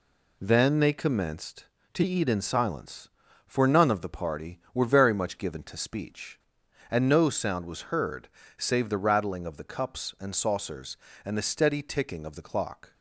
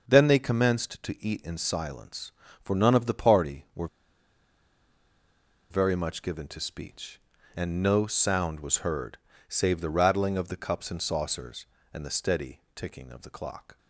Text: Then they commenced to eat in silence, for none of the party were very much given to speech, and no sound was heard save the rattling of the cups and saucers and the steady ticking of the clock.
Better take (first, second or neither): first